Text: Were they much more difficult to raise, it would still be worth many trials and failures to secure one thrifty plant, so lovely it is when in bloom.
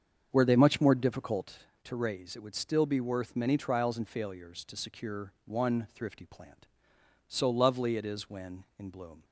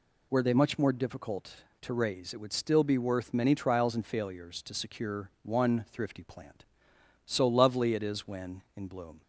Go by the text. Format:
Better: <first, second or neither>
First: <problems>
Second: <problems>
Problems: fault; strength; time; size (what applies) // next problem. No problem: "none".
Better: second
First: starts louder than the rest; strong; until 1.6 s; 7 dB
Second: none